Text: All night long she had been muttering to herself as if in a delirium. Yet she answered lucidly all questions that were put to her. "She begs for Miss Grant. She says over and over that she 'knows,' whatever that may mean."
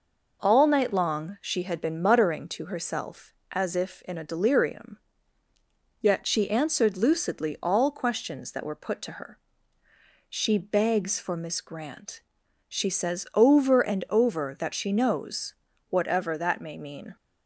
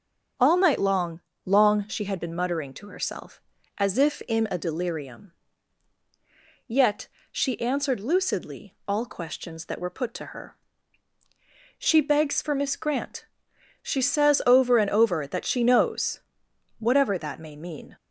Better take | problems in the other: first | starts louder than the rest; until 1.6 s; 7 dB // says "long" twice; at 1.4 s // pauses between "Yet" and "she"; slight; at 7.0 s; 0.24 s long

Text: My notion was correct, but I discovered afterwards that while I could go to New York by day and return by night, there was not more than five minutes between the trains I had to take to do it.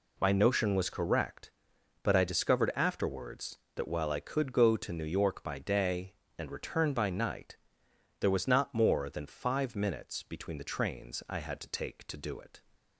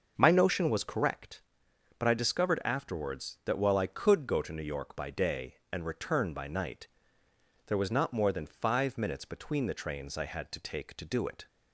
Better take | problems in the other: first | starts louder than the rest; until 1.1 s; 6.5 dB

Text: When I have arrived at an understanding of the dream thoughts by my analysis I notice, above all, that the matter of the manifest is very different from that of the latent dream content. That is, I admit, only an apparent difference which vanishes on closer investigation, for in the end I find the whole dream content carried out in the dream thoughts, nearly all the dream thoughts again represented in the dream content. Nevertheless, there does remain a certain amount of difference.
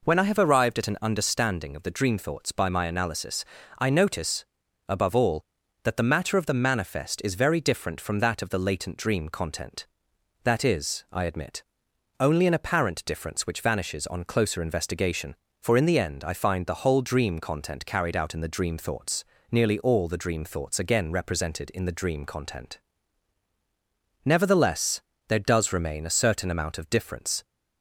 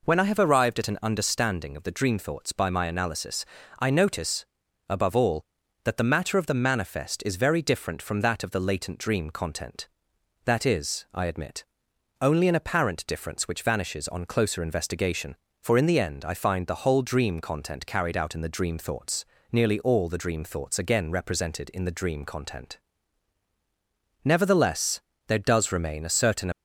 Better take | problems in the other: first | pauses between "analysis" and "I"; slight; at 3.4 s; 0.32 s long; slight in the first // stops before "amount of difference"; at 26.5 s

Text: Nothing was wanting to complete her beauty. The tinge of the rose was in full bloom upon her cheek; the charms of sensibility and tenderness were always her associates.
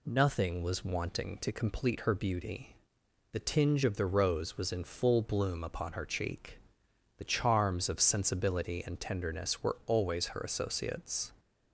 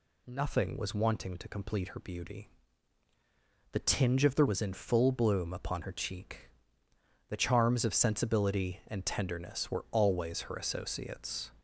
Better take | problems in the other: first | skips "rose"; at 4.4 s

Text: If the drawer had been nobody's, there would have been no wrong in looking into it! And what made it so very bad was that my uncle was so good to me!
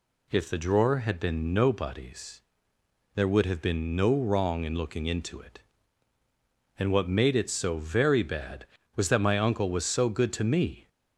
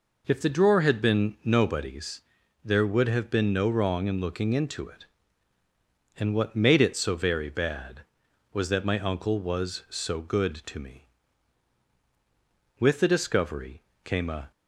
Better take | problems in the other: first | goes on to say "With the discovery came a"; strong; from 12.7 s on; 1.7 s long

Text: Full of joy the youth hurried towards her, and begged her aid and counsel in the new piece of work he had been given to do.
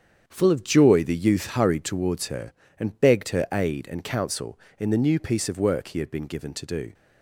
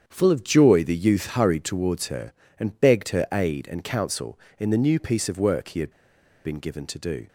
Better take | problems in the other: first | starts louder than the rest; strong; until 1.0 s; 7.5 dB; strong in the first // pauses between "had" and "been"; noticeable; at 5.9 s; 0.52 s long

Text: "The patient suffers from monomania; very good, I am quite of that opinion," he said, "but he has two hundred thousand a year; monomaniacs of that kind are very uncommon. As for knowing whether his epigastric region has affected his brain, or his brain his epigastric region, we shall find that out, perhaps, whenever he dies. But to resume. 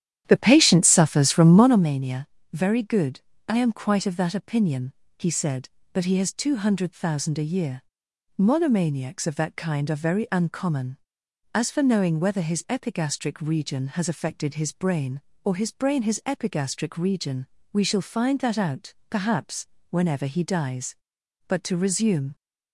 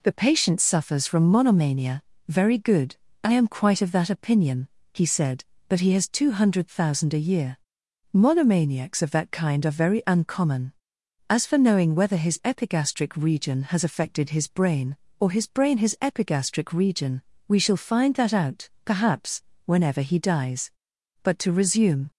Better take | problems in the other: second | starts louder than the rest; strong; until 1.9 s; 10.5 dB

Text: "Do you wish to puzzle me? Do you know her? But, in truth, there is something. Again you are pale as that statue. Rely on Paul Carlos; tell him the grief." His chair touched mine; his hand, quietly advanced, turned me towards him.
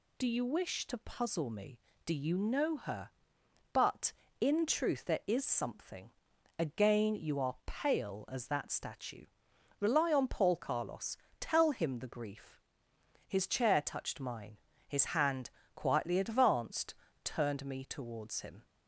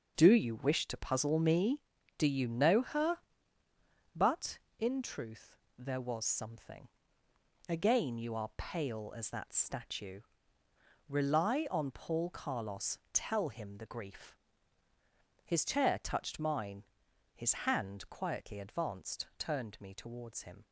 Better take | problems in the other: first | starts louder than the rest; noticeable; until 1.1 s; 6 dB // says "was" for "is"; at 6.0 s // pauses between "his" and "hand"; slight; at 17.5 s; 0.16 s long

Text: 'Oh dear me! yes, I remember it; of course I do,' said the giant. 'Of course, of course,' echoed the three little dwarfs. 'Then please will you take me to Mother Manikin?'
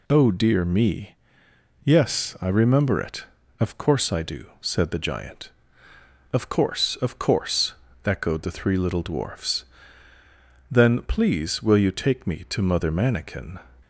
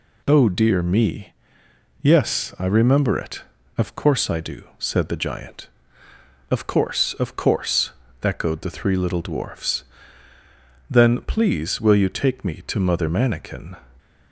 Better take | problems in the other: neither | none

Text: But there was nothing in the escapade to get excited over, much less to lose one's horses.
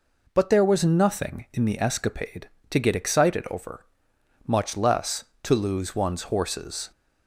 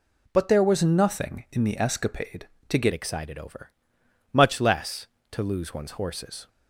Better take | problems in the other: first | changes voice at "excited"; from 2.9 s on; 3.5 s long

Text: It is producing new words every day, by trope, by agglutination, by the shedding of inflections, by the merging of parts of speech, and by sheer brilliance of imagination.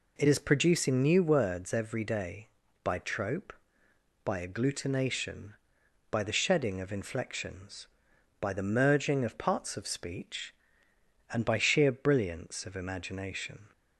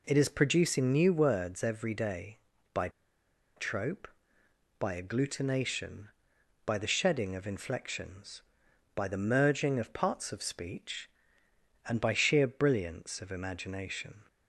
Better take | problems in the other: first | pauses between "by" and "trope"; noticeable; at 2.8 s; 0.67 s long

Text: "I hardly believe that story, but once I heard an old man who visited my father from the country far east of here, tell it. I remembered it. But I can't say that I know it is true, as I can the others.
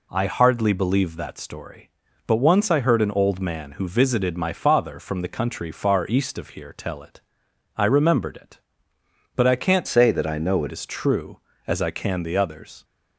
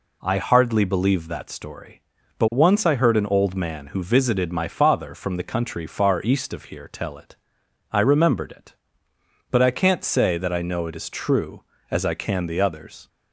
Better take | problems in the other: second | changes voice from "say" to "it"; from 9.8 to 10.7 s; 0.9 s long

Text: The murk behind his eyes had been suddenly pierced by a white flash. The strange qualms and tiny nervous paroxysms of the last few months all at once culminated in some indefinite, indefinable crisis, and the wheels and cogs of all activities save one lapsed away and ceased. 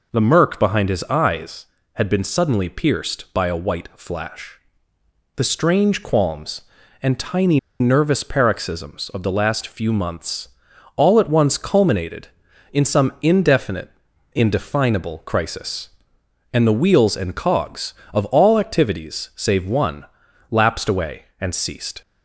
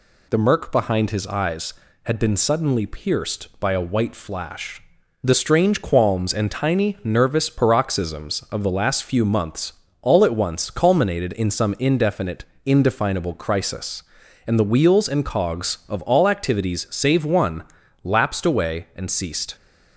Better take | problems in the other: second | pauses between "tiny" and "nervous"; slight; at 7.5 s; 0.20 s long // pauses between "months" and "all"; noticeable; at 10.4 s; 0.48 s long; slight in the second // pauses between "one" and "lapsed"; noticeable; at 20.0 s; 0.46 s long; also in the second

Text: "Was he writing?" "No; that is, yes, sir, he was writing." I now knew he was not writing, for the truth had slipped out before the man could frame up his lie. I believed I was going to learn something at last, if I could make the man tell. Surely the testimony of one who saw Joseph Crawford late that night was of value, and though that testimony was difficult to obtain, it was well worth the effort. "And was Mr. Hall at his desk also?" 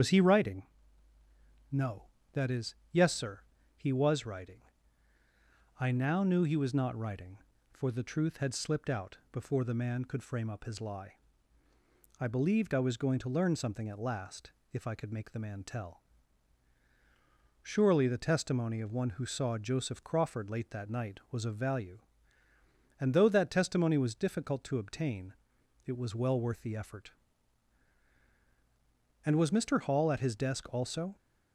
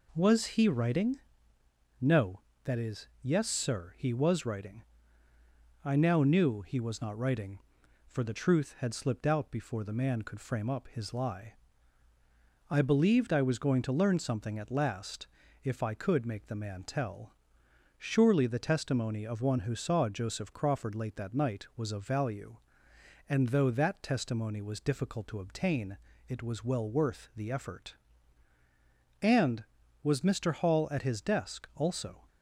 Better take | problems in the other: second | loses the start of "Was"; at 0.0 s; 85 ms // starts louder than the rest; strong; until 2.0 s; 7.5 dB

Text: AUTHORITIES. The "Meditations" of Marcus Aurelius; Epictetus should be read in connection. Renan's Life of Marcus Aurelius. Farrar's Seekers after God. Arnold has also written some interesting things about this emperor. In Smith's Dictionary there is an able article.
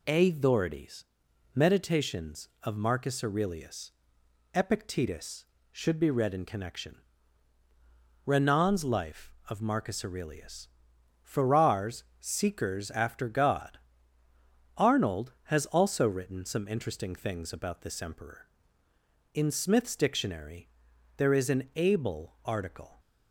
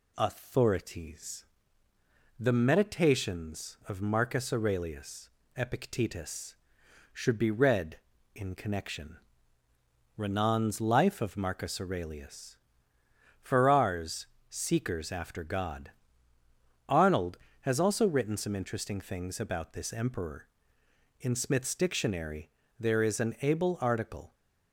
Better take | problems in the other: second | skips "The"; at 1.2 s // pauses between "Farrar's" and "Seekers"; slight; at 12.0 s; 0.16 s long; slight in the second // pauses between "Dictionary" and "there"; noticeable; at 20.6 s; 0.48 s long; slight in the second

